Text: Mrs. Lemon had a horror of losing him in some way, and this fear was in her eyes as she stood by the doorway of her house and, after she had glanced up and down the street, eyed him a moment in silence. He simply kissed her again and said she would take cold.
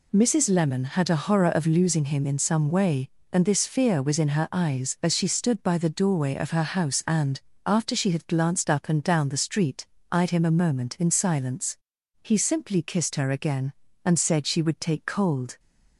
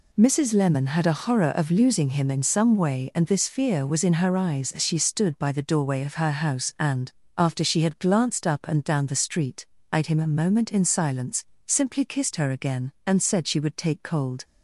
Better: first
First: none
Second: skips "He"; at 11.5 s

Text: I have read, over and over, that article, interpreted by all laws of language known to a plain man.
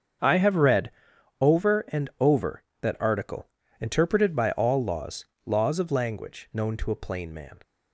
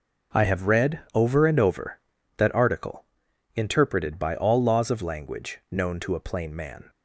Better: second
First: starts louder than the rest; strong; until 1.7 s; 7 dB // says "laws" twice; at 5.4 s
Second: none

